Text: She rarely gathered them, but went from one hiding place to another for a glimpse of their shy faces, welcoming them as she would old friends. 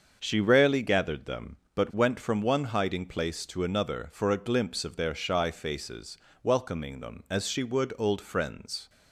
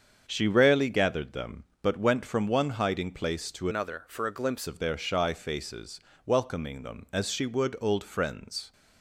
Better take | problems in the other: first | starts louder than the rest; strong; until 1.2 s; 7 dB; also in the first // changes voice from "another" to "glimpse"; from 3.6 to 4.6 s; 1.0 s long

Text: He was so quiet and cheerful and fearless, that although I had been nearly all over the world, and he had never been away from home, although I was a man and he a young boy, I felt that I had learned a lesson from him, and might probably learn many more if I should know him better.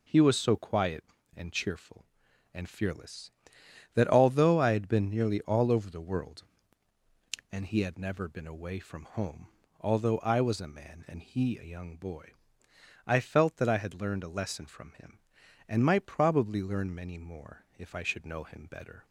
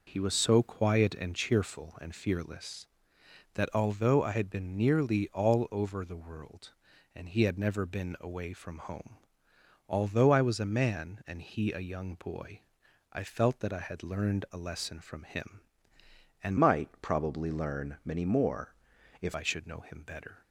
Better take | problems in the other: first | changes voice from "might" to "if"; from 16.5 to 19.3 s; 2.8 s long // pauses between "more" and "if"; noticeable; at 18.7 s; 0.48 s long

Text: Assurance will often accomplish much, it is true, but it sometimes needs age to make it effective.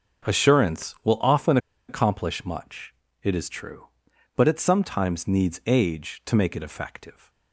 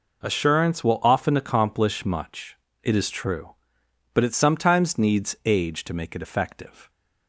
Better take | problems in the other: second | starts louder than the rest; until 1.3 s; 6.5 dB // pauses between "often" and "accomplish"; slight; at 1.5 s; 0.31 s long

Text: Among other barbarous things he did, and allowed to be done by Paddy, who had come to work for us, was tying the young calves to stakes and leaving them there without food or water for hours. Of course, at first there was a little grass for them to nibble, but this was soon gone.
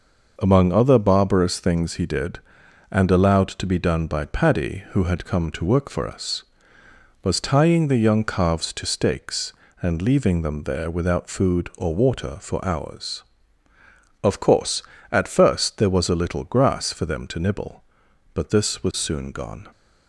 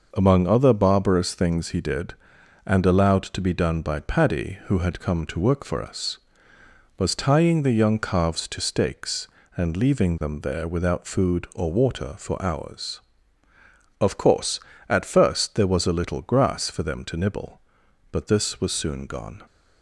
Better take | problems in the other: neither | none

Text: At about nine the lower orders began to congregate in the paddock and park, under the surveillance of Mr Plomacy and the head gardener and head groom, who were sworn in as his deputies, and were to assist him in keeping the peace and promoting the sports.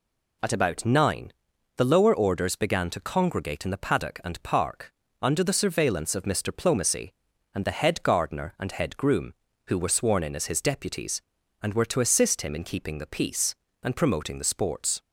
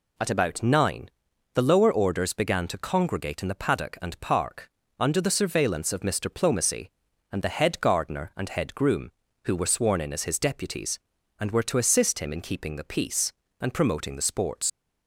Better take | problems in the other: first | pauses between "nine" and "the"; at 1.0 s; 0.44 s long; also in the first // leaves "sports" unfinished; at 14.6 s; 85 ms

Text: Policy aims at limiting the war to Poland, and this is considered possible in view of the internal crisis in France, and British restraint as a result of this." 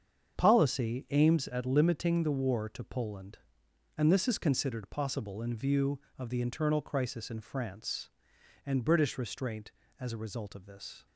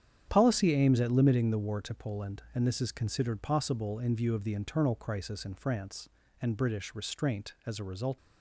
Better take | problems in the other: first | starts louder than the rest; strong; until 1.2 s; 9 dB; strong in the first // stops before "of this"; at 8.1 s

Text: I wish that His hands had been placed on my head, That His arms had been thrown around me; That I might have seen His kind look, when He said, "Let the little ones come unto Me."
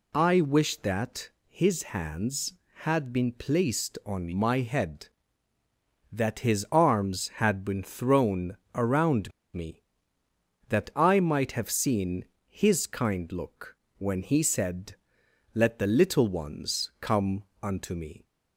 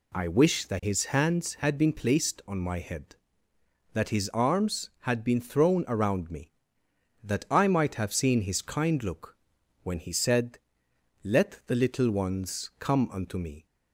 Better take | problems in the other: second | pauses between "that" and "His"; slight; at 1.2 s; 0.20 s long // pauses between "thrown" and "around"; slight; at 8.5 s; 0.16 s long // pauses between "around" and "me"; slight; at 9.3 s; 0.23 s long // pauses between "seen" and "His"; slight; at 12.2 s; 0.24 s long // pauses between "come" and "unto"; slight; at 17.4 s; 0.18 s long

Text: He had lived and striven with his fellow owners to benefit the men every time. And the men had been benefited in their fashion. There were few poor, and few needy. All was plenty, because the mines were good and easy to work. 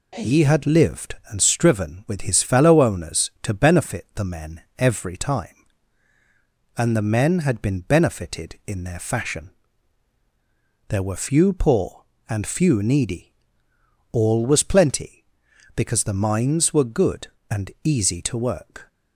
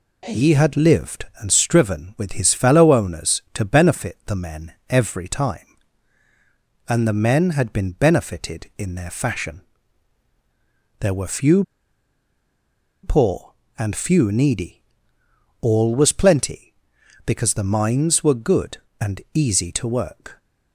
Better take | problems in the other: first | pauses between "men" and "every"; slight; at 4.7 s; 0.16 s long; slight in the first // pauses between "few" and "poor"; strong; at 11.6 s; 1.3 s long

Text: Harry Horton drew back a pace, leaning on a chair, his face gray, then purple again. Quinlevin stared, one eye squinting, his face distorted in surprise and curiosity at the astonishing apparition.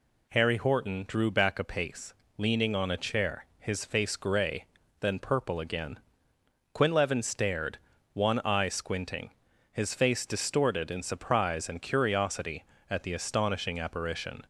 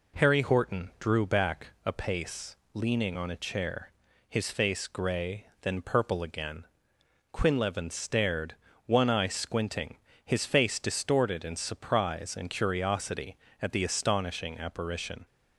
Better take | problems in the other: neither | none

